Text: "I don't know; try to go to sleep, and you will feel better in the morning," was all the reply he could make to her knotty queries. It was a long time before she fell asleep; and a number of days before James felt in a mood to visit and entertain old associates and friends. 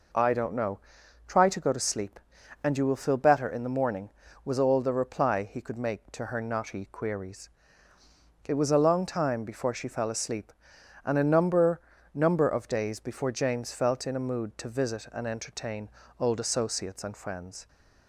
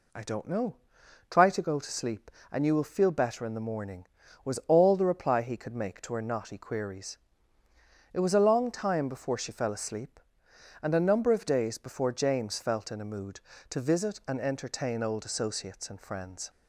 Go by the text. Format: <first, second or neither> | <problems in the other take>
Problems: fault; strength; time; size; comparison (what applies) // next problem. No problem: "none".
second | says "number" twice; at 12.1 s // pauses between "entertain" and "old"; slight; at 15.8 s; 0.30 s long